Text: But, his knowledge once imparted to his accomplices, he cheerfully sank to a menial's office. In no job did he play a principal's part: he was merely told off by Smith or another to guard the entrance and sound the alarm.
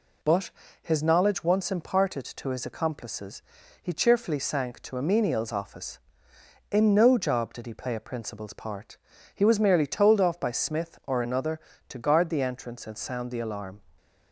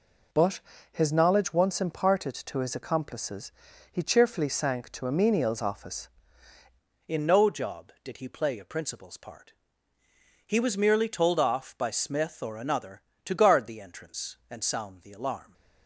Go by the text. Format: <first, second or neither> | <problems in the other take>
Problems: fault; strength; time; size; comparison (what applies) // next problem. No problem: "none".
first | changes voice at "In"; from 7.0 s on; 8.5 s long